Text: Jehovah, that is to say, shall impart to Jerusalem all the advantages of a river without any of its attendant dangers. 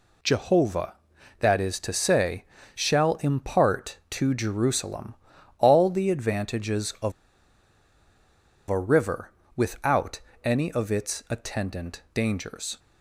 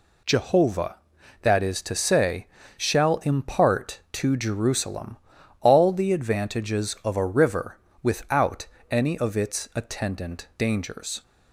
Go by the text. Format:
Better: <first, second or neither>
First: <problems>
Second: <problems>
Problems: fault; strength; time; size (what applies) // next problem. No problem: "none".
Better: second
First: pauses between "Jerusalem" and "all"; at 5.1 s; 0.44 s long // pauses between "of" and "a"; strong; at 7.1 s; 1.5 s long // pauses between "river" and "without"; slight; at 9.3 s; 0.24 s long // pauses between "without" and "any"; slight; at 10.2 s; 0.22 s long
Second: pauses between "Jerusalem" and "all"; at 5.1 s; 0.44 s long // pauses between "river" and "without"; slight; at 7.7 s; 0.24 s long // pauses between "without" and "any"; slight; at 8.6 s; 0.22 s long